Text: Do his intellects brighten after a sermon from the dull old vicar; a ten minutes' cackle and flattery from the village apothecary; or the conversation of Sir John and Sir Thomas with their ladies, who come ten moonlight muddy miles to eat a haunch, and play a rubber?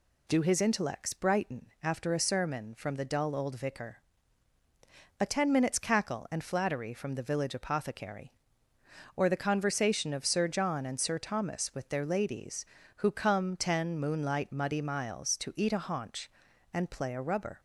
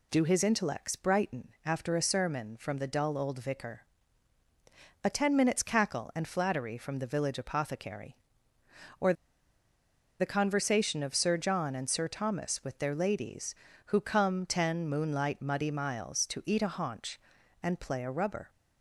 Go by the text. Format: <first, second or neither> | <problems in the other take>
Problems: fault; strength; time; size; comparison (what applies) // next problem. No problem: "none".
first | pauses between "or" and "the"; at 9.1 s; 1.0 s long